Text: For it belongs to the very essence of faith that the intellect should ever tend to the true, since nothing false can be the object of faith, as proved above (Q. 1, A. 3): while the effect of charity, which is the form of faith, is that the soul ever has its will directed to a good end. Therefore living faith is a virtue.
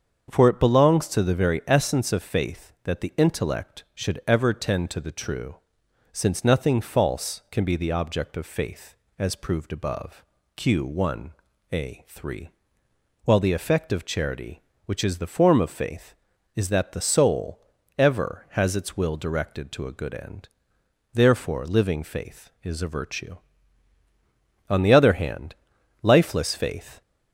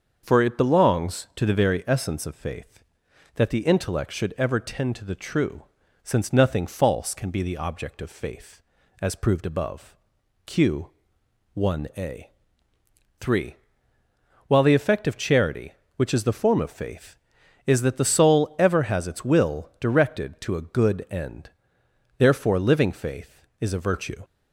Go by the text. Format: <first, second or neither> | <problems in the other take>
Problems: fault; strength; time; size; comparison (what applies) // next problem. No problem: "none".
second | starts louder than the rest; until 1.3 s; 7 dB; also in the second // pauses between "soul" and "ever"; at 17.5 s; 0.38 s long // goes on to say "On the other hand lifeless faith"; strong; from 24.6 s on; 2.3 s long